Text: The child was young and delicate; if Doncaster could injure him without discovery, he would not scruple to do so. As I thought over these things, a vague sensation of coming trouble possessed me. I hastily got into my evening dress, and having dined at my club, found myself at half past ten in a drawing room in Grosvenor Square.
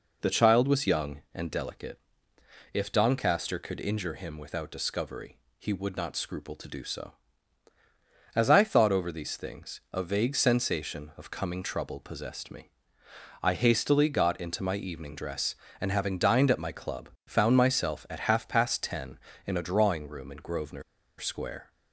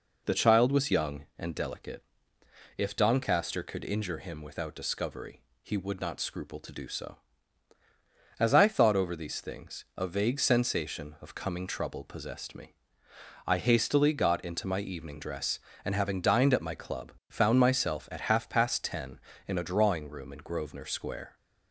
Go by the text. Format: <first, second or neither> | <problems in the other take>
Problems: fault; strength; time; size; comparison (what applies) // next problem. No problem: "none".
second | pauses between "Grosvenor" and "Square"; at 20.8 s; 0.36 s long